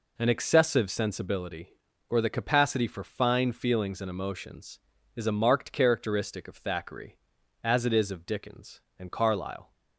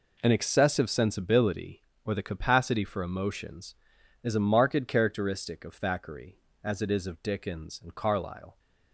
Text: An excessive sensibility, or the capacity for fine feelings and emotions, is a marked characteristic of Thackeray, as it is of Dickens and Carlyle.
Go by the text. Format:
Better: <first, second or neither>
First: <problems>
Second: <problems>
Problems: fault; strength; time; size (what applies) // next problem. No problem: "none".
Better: first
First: none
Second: skips "fine feelings and"; at 3.0 s